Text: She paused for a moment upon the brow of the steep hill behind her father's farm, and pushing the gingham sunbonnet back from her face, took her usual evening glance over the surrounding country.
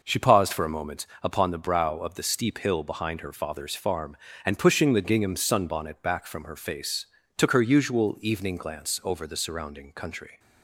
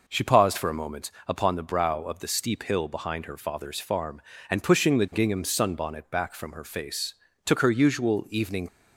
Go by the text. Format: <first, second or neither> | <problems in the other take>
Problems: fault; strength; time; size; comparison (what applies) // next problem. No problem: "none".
first | pauses between "moment" and "upon"; slight; at 1.1 s; 0.16 s long; slight in the first // stops before "glance over the surrounding country"; at 8.6 s